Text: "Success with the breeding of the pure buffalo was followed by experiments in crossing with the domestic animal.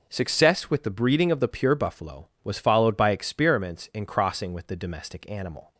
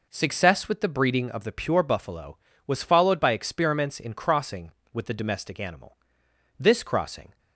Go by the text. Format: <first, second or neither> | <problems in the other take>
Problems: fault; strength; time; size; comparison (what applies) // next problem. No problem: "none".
first | goes on to say "This crossing"; noticeable; from 6.5 s on; 0.80 s long